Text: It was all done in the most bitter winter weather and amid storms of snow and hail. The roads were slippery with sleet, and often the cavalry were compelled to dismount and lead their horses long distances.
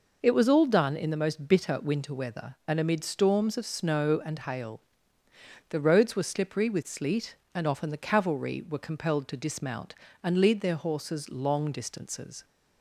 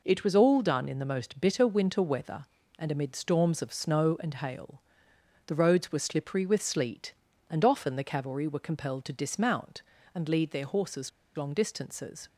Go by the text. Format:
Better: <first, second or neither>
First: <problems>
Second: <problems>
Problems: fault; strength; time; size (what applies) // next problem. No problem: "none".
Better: first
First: none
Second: pauses between "horses" and "long"; slight; at 11.1 s; 0.27 s long